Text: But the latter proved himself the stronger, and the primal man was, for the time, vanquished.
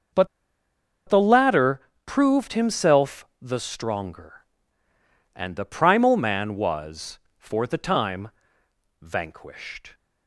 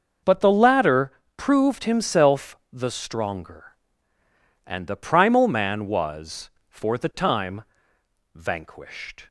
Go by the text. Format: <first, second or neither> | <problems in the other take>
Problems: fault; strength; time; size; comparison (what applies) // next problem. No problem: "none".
second | starts louder than the rest; noticeable; until 2.2 s; 6 dB; noticeable in the second // pauses between "But" and "the"; noticeable; at 0.2 s; 0.80 s long // pauses between "latter" and "proved"; slight; at 1.7 s; 0.26 s long; slight in the second